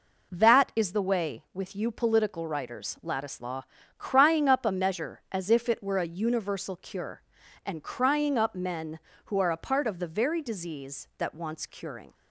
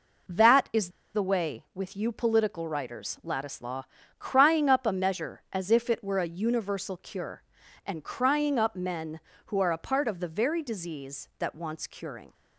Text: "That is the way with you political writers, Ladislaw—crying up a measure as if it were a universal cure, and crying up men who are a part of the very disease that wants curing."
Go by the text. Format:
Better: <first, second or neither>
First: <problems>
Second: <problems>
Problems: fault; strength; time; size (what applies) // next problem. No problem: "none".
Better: first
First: none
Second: pauses between "is" and "the"; slight; at 0.8 s; 0.25 s long